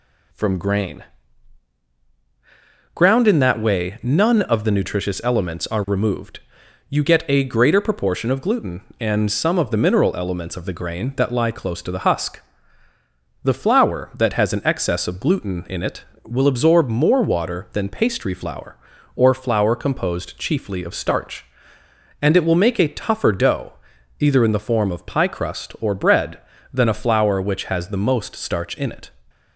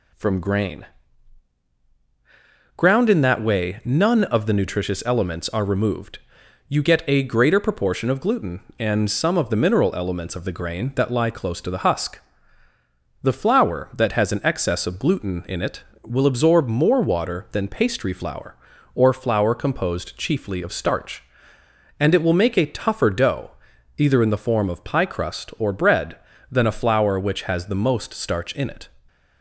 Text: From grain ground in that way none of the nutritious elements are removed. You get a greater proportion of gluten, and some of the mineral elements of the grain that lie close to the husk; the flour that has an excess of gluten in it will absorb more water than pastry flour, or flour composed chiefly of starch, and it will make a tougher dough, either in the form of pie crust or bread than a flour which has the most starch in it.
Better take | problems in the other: neither | pauses between "grain" and "ground"; strong; the same in both

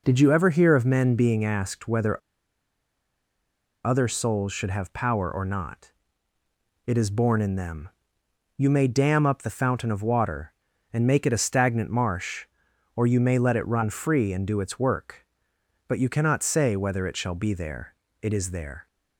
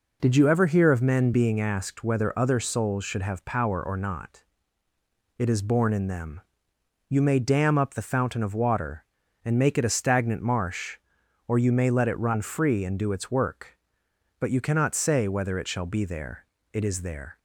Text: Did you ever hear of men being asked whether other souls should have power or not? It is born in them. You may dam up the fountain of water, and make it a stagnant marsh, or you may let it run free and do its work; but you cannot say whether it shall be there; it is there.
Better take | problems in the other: second | pauses between "whether" and "other"; strong; at 2.2 s; 1.6 s long

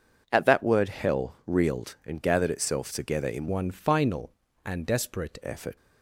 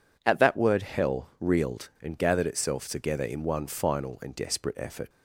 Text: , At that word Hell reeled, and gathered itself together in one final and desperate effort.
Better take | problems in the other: second | changes voice from "one" to "desperate"; from 3.4 to 5.3 s; 1.9 s long

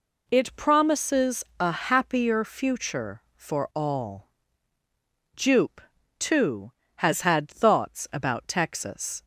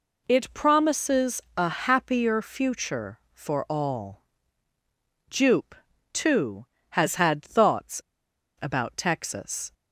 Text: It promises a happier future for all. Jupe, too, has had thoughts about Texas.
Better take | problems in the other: first | pauses between "promises" and "a"; slight; at 1.4 s; 0.16 s long; slight in the first // pauses between "thoughts" and "about"; noticeable; at 7.9 s; 0.61 s long

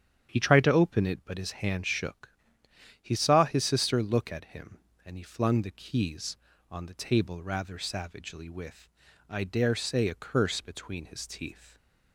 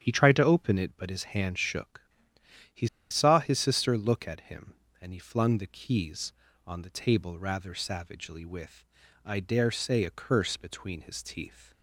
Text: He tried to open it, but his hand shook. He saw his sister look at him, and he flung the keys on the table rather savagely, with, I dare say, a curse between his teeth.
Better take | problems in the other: first | starts louder than the rest; strong; until 1.0 s; 9 dB; strong in the first // pauses between "He" and "saw"; slight; at 2.8 s; 0.22 s long

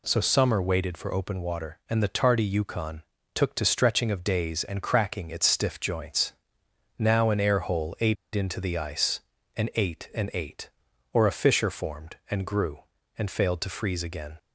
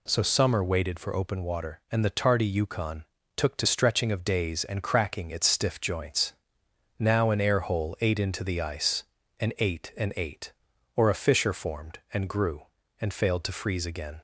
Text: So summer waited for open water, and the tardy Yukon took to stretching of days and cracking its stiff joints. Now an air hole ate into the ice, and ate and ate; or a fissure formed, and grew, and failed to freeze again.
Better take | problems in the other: second | pauses between "Yukon" and "took"; slight; at 3.0 s; 0.32 s long; slight in the second // pauses between "ate" and "into"; slight; at 8.1 s; 0.20 s long

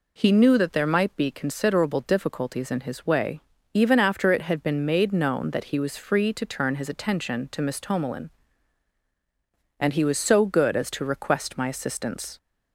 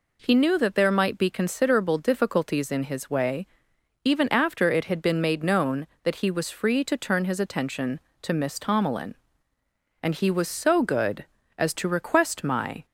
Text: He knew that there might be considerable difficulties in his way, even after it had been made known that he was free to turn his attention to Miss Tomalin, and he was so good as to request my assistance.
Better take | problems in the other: first | stops before "assistance"; at 12.8 s

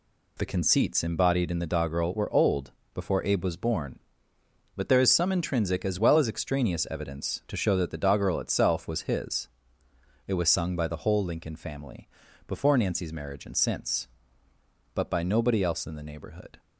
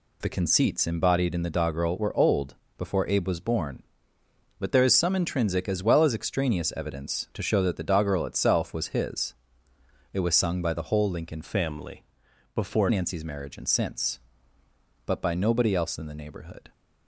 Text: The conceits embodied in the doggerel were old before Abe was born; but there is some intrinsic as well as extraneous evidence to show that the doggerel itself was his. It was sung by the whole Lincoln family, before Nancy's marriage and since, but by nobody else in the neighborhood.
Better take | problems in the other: first | pauses between "old" and "before"; slight; at 2.5 s; 0.24 s long; slight in the first // changes voice from "family" to "before"; from 11.4 to 12.8 s; 1.4 s long

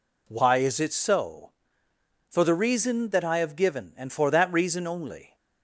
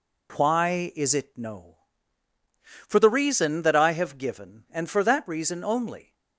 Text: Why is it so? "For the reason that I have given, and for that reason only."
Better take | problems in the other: first | says "no" for "so"; at 1.3 s

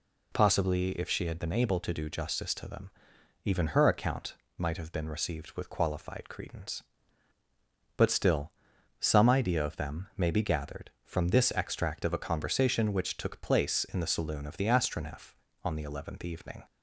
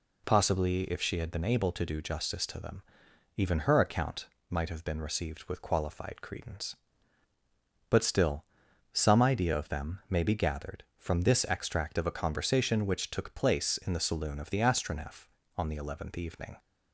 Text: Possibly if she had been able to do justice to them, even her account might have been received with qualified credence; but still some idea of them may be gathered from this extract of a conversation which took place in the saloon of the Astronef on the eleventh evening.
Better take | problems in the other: neither | pauses between "account" and "might"; slight; the same in both // pauses between "still" and "some"; noticeable; the same in both

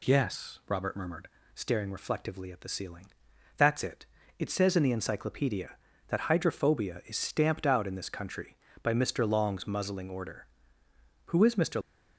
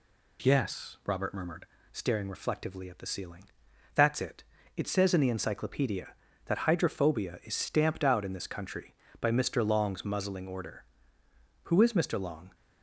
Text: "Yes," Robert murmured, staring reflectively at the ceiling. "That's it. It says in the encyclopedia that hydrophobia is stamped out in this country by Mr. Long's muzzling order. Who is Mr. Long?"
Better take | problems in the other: second | stops before "Long"; at 11.8 s

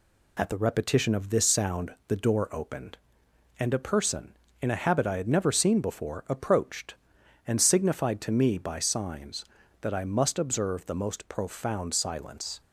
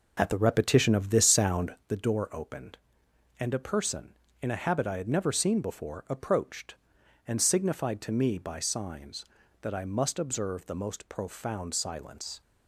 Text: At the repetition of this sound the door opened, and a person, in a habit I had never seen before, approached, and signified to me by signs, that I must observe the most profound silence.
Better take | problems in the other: first | starts louder than the rest; noticeable; until 1.9 s; 5 dB

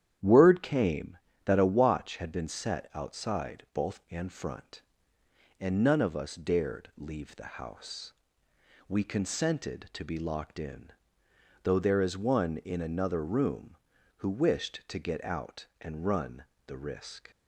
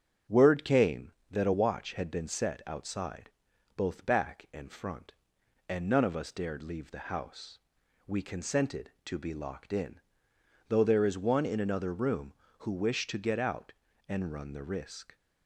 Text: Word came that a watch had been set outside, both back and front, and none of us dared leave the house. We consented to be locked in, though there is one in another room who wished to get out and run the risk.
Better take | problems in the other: second | starts louder than the rest; strong; until 1.5 s; 10 dB; strong in the second // skips "back"; at 4.0 s // pauses between "run" and "the"; slight; at 16.4 s; 0.22 s long

